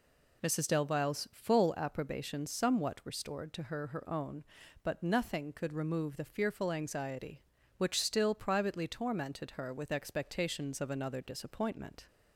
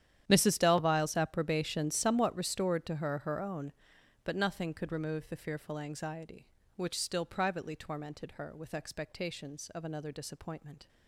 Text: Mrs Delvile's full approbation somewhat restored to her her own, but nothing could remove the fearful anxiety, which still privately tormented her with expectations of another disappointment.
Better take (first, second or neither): first